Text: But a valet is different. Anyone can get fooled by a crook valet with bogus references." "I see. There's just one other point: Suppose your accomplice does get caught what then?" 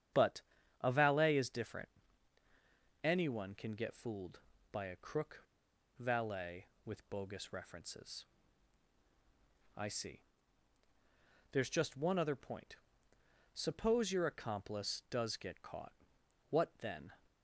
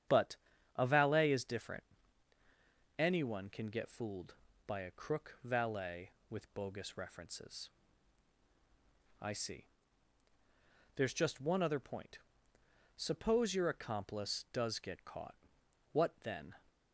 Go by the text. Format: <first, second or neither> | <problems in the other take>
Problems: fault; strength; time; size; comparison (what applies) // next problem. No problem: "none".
second | starts louder than the rest; strong; until 1.5 s; 9 dB; strong in the second // pauses between "But" and "a"; at 0.4 s; 0.38 s long; also in the second // pauses between "crook" and "valet"; noticeable; at 5.4 s; 0.56 s long // pauses between "caught" and "what"; noticeable; at 15.9 s; 0.56 s long; noticeable in the second